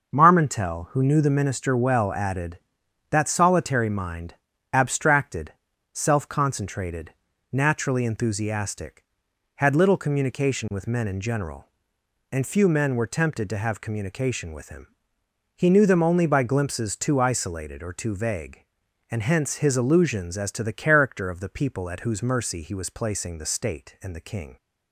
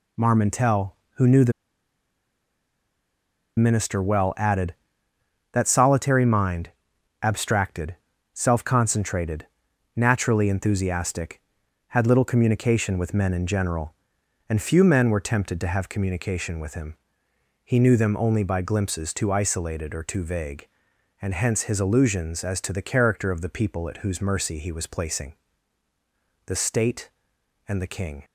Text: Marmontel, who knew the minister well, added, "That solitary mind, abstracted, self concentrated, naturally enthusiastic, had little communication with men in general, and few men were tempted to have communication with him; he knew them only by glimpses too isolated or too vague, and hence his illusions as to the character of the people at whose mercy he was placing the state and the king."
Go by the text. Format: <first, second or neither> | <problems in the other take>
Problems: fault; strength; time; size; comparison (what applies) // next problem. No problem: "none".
first | pauses between "the" and "minister"; strong; at 1.5 s; 2.0 s long // pauses between "placing" and "the"; at 25.3 s; 1.1 s long